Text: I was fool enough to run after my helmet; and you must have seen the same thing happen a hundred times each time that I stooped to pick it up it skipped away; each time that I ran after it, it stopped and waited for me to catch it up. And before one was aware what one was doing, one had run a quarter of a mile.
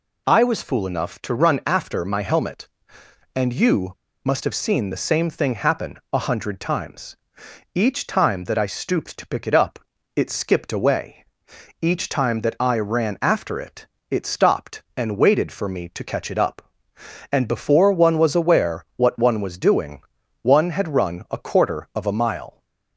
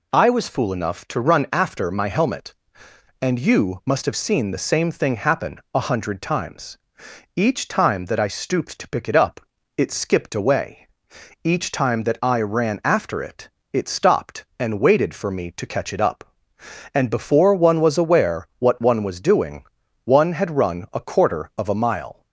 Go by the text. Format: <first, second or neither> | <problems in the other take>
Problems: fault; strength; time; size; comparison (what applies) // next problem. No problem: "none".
second | pauses between "you" and "must"; slight; at 3.9 s; 0.26 s long // pauses between "happen" and "a"; slight; at 5.9 s; 0.16 s long; slight in the second // pauses between "times" and "each"; noticeable; at 7.1 s; 0.58 s long; noticeable in the second // pauses between "up" and "it"; at 9.7 s; 0.38 s long; also in the second